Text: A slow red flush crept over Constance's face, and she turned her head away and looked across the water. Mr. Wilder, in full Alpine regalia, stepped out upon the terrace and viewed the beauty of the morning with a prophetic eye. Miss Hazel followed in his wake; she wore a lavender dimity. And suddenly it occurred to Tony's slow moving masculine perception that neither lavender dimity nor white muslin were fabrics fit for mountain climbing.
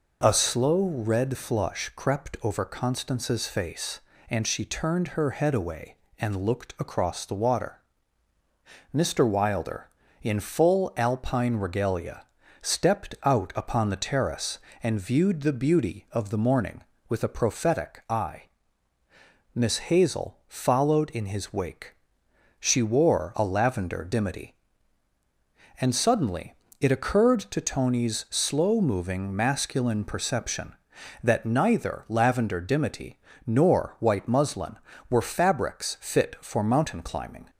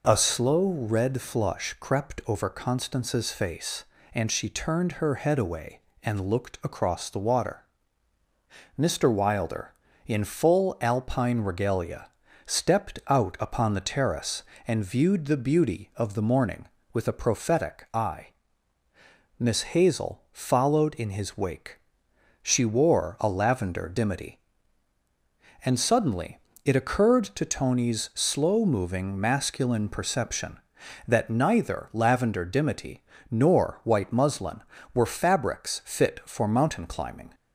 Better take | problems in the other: neither | pauses between "suddenly" and "it"; slight; the same in both // pauses between "dimity" and "nor"; slight; the same in both

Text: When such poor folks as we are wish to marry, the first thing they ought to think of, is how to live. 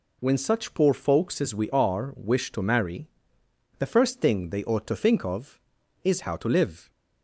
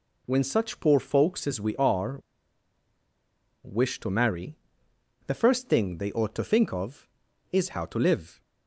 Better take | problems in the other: first | pauses between "are" and "wish"; strong; at 2.1 s; 1.4 s long

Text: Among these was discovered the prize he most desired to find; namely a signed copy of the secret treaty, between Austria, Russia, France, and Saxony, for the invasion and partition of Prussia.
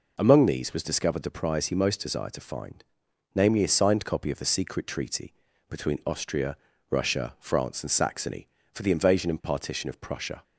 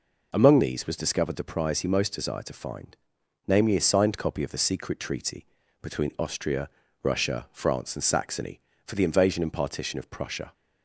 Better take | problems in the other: neither | none

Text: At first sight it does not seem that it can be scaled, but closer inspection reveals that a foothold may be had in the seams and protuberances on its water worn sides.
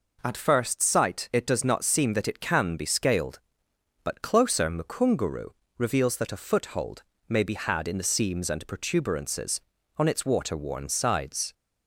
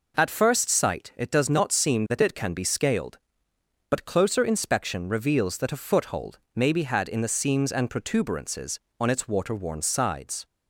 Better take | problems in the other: second | says "mukunguru" for "inspection"; at 4.6 s // pauses between "foothold" and "may"; slight; at 7.0 s; 0.26 s long; slight in the second

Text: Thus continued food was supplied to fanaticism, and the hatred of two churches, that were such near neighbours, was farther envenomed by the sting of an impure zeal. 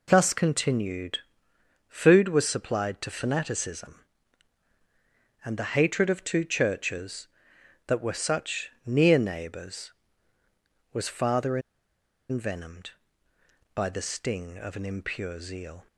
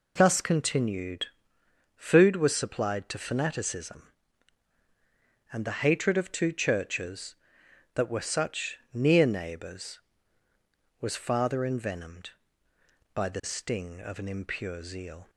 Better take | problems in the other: second | pauses between "continued" and "food"; noticeable; at 1.1 s; 0.68 s long; noticeable in the second // pauses between "such" and "near"; slight; at 8.7 s; 0.16 s long; slight in the second // pauses between "farther" and "envenomed"; noticeable; at 11.5 s; 0.70 s long

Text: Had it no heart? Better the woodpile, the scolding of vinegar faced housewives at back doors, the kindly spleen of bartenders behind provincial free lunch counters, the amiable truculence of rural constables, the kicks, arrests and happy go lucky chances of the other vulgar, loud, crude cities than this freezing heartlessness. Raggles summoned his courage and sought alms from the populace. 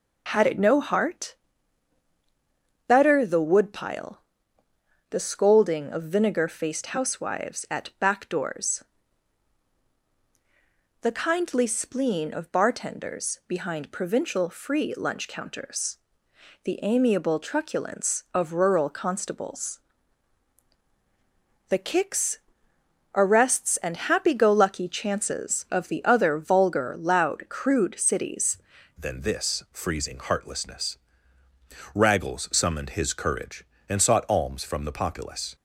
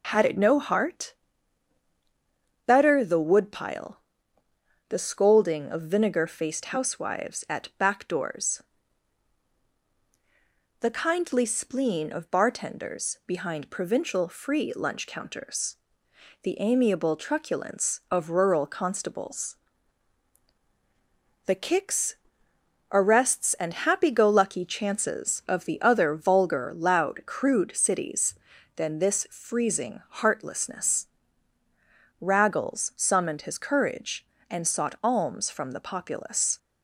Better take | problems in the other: second | changes voice at "than"; from 28.9 s on; 6.6 s long

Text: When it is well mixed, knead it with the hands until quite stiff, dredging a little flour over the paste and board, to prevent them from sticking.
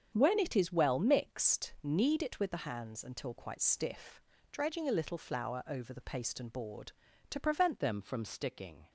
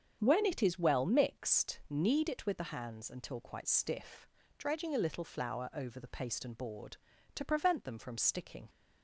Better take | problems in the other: second | starts louder than the rest; strong; until 1.1 s; 8 dB; strong in the second // changes voice at "them"; from 7.7 s on; 1.1 s long

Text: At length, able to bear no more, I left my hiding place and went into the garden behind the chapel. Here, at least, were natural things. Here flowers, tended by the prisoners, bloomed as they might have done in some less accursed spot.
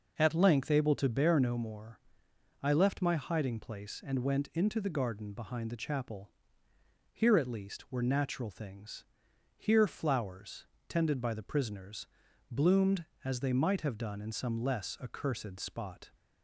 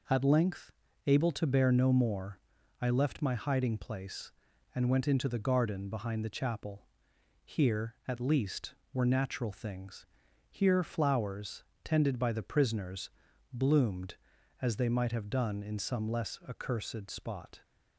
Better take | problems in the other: neither | none

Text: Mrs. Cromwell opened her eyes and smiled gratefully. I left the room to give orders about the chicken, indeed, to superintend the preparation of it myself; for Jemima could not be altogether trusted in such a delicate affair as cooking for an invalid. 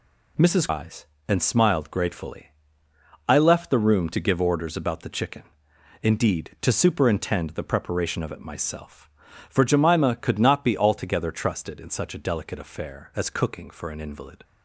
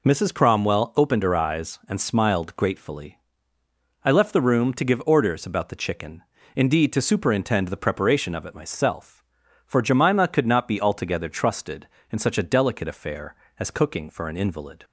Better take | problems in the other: second | skips "Cromwell opened her"; at 0.6 s

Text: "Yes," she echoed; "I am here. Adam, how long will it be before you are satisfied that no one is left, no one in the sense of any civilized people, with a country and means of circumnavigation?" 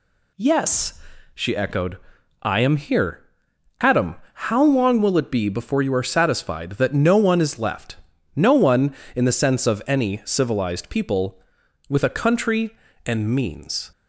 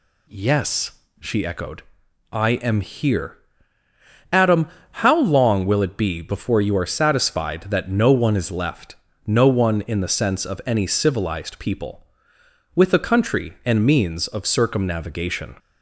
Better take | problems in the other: second | stops before "of circumnavigation"; at 13.9 s

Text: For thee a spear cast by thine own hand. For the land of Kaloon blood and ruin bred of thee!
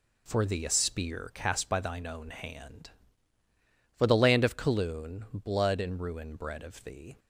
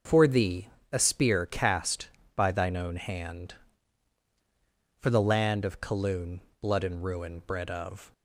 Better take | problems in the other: first | starts louder than the rest; noticeable; until 1.3 s; 6 dB // pauses between "thee" and "a"; slight; at 0.6 s; 0.24 s long // pauses between "Kaloon" and "blood"; slight; at 6.3 s; 0.22 s long // stops before "thee"; at 8.1 s

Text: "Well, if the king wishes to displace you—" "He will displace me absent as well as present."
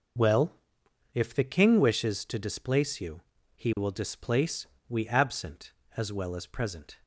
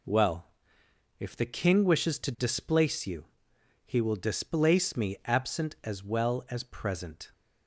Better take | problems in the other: second | says "we" for "me"; at 4.8 s

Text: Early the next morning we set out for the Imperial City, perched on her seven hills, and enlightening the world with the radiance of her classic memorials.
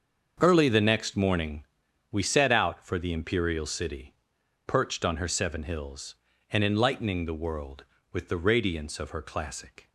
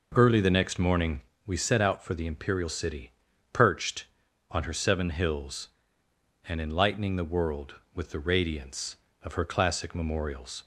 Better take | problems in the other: second | starts louder than the rest; until 1.4 s; 6.5 dB // pauses between "morning" and "we"; noticeable; at 1.6 s; 0.48 s long; slight in the second // stops before "memorials"; at 9.8 s

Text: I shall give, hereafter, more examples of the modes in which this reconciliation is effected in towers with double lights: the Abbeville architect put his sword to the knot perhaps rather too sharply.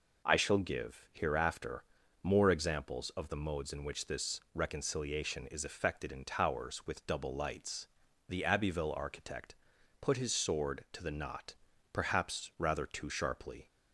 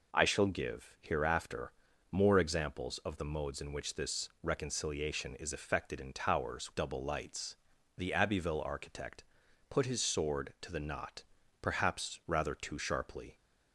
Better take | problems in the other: first | skips "with"; at 6.7 s // pauses between "architect" and "put"; noticeable; at 9.2 s; 0.46 s long; noticeable in the first // pauses between "knot" and "perhaps"; at 11.2 s; 0.38 s long; also in the first

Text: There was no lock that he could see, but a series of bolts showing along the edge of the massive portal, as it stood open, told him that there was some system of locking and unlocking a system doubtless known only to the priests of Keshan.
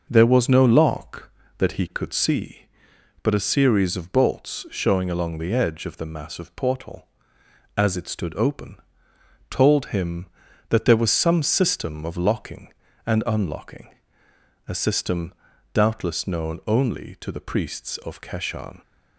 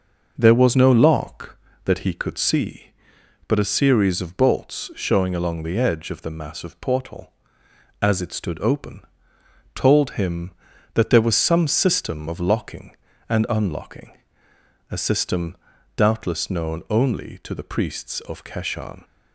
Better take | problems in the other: neither | pauses between "unlocking" and "a"; noticeable; the same in both // pauses between "system" and "doubtless"; the same in both

